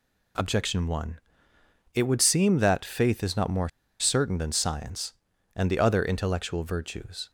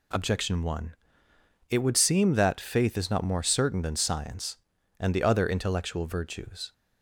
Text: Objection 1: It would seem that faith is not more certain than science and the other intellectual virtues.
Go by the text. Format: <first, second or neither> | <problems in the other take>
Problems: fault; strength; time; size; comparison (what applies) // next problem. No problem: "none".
second | pauses between "more" and "certain"; slight; at 3.6 s; 0.30 s long